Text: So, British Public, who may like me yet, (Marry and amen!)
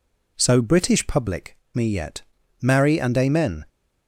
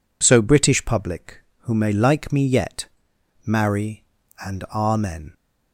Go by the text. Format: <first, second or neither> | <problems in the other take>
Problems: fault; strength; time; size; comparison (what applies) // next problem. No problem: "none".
second | skips "who may like"; at 1.6 s